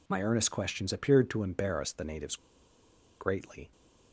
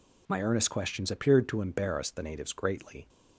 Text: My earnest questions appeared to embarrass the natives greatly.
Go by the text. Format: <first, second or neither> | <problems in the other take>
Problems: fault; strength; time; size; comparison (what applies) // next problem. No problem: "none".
second | pauses between "natives" and "greatly"; noticeable; at 2.3 s; 0.82 s long